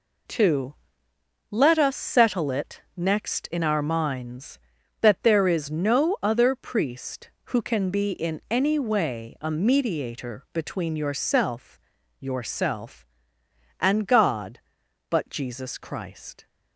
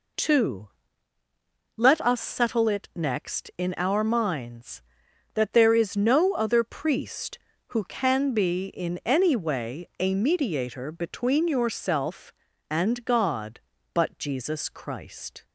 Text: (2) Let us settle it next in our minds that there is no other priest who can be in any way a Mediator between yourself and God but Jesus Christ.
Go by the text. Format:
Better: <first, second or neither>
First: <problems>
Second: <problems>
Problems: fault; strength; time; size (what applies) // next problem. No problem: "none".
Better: second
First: says "yourself" twice; at 12.1 s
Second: none